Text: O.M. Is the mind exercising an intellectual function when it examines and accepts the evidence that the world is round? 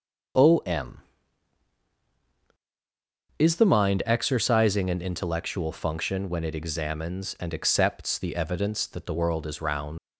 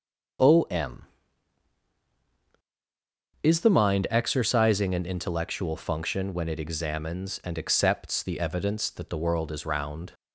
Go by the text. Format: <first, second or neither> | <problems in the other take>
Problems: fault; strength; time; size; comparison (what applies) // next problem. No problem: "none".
second | starts louder than the rest; until 3.8 s; 7 dB; also in the second // leaves "round" unfinished; at 9.9 s; 115 ms